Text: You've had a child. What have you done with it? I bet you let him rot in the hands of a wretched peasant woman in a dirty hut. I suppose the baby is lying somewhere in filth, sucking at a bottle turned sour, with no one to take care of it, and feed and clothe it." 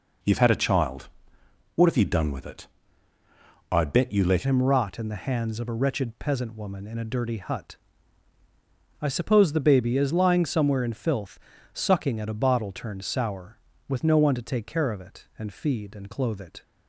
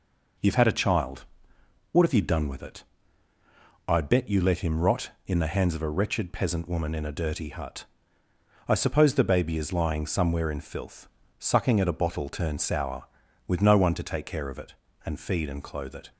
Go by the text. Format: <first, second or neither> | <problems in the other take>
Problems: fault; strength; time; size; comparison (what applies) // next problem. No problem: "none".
second | changes voice at "him"; from 4.4 s on; 12.2 s long